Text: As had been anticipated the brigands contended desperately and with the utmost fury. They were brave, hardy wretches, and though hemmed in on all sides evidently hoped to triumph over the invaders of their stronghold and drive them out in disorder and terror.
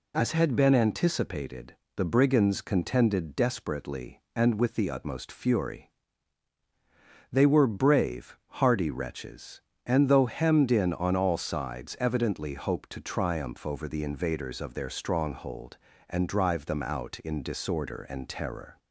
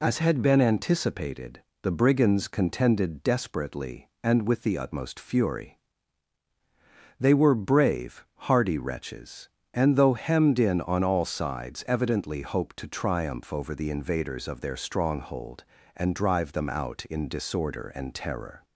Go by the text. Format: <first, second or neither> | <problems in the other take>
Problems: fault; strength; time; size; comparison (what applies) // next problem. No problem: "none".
neither | pauses between "anticipated" and "the"; slight; the same in both